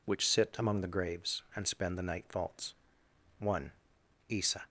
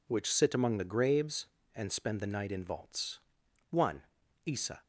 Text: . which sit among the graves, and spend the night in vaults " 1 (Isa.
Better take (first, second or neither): second